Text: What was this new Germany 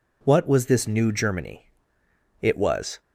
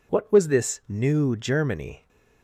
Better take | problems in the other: second | goes on to say "It was"; from 2.4 s on; 0.58 s long

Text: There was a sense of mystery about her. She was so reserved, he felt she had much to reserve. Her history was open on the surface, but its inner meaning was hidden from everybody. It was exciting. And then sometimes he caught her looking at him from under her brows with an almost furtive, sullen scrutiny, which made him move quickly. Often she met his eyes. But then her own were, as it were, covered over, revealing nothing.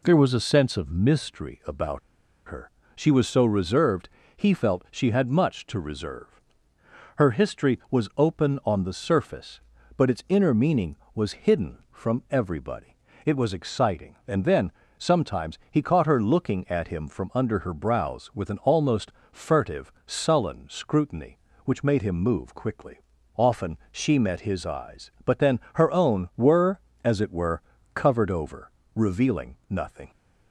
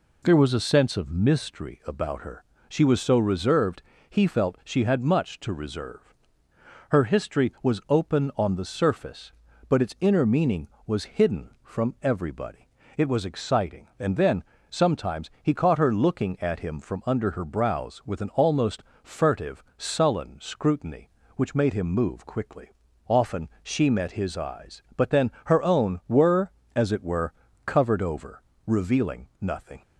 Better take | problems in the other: second | pauses between "about" and "her"; noticeable; at 1.9 s; 0.48 s long // pauses between "then" and "sometimes"; slight; at 14.7 s; 0.26 s long; slight in the second // pauses between "almost" and "furtive"; slight; at 19.1 s; 0.18 s long; slight in the second // pauses between "Often" and "she"; slight; at 23.7 s; 0.16 s long; slight in the second

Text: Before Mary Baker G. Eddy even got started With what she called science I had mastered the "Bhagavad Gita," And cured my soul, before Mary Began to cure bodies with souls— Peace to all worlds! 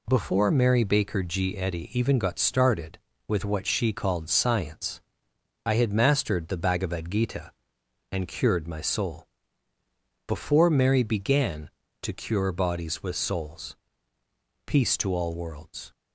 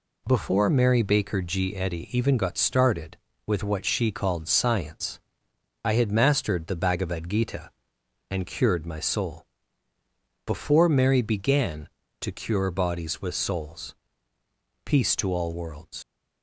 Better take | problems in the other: first | pauses between "science" and "I"; noticeable; at 5.1 s; 0.64 s long; noticeable in the first // leaves "worlds" unfinished; at 16.0 s; 85 ms

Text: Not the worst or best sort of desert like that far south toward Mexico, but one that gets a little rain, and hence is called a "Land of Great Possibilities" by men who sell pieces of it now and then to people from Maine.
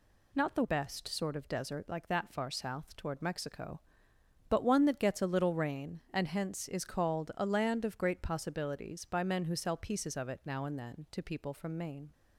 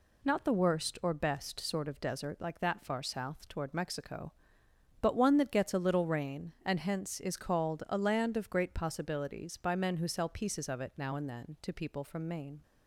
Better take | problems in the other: second | skips "worst or"; at 0.6 s

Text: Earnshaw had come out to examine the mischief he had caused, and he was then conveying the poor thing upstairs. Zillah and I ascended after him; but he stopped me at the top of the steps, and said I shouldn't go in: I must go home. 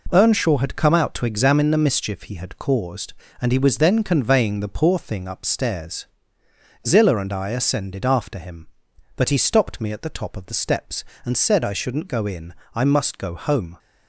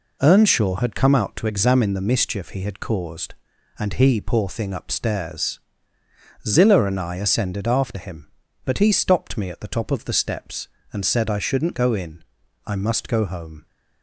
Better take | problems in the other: first | skips "was then conveying the"; at 4.1 s

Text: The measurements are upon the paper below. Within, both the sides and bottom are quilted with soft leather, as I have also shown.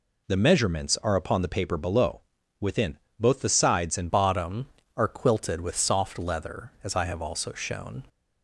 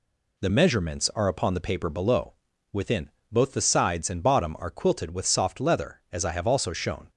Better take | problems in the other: second | changes voice at "bottom"; from 4.0 s on; 4.0 s long

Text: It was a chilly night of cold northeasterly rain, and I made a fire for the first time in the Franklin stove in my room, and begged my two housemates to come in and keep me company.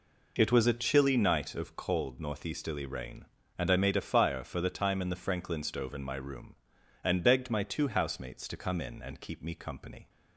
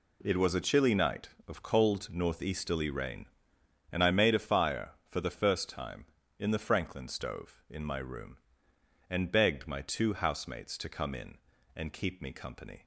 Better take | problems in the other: second | skips "first"; at 4.6 s

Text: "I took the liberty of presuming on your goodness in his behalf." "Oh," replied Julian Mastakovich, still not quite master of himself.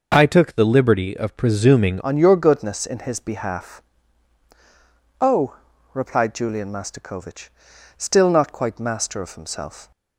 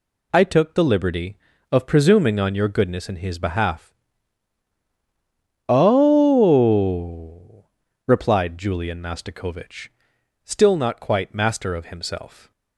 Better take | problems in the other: second | changes voice at "on"; from 2.0 s on; 7.9 s long

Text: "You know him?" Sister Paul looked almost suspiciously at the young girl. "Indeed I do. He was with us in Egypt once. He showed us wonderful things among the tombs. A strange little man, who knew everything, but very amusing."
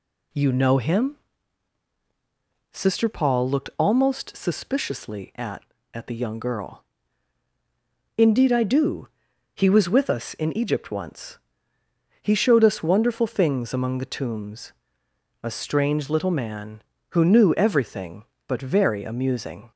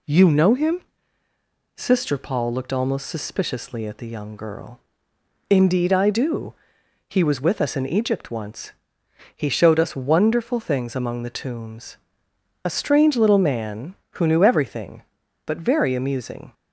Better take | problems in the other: second | says "at" twice; at 5.9 s

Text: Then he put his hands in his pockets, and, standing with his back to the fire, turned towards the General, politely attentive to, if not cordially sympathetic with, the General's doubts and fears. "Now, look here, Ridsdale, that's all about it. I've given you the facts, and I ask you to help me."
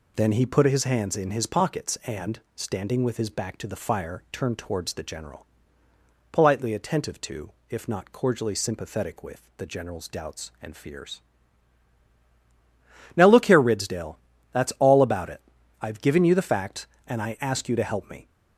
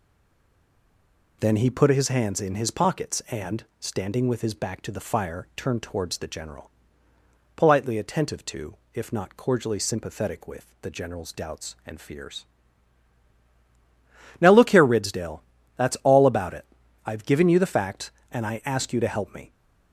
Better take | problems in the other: first | stays silent before the first word; noticeable; until 1.4 s; 1.4 s long

